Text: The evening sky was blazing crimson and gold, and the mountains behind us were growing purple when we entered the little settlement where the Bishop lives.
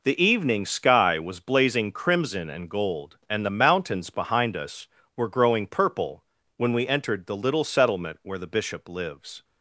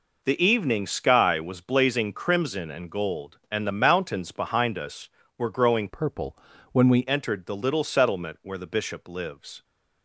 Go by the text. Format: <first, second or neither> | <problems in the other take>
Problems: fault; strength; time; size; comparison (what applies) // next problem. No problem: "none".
first | changes voice from "purple" to "we"; from 5.8 to 7.0 s; 1.2 s long // pauses between "purple" and "when"; slight; at 6.3 s; 0.36 s long; slight in the first